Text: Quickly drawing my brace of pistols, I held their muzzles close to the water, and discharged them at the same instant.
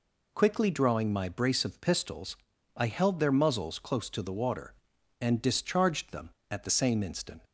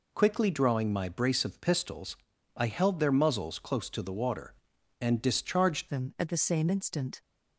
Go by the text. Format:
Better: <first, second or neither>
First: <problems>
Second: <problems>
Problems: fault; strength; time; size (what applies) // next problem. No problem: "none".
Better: first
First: none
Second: changes voice at "them"; from 5.8 s on; 1.4 s long